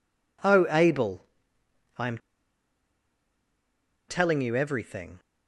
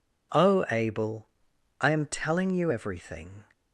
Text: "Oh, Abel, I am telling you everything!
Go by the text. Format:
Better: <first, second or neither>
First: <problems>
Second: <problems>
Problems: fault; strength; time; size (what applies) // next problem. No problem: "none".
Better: second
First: pauses between "am" and "telling"; strong; at 2.1 s; 1.9 s long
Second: none